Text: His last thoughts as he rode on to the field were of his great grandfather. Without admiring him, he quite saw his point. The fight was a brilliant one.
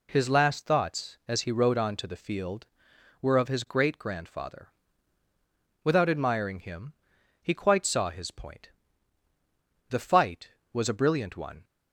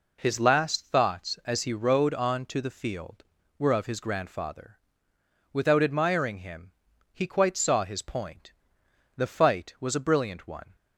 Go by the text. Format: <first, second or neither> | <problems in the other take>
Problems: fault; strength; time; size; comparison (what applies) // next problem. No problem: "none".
first | skips "great"; at 4.0 s